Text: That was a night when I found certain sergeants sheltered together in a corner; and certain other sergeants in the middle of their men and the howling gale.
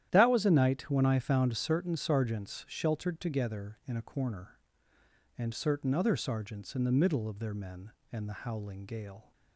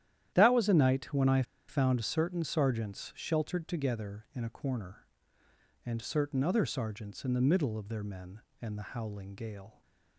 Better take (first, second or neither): first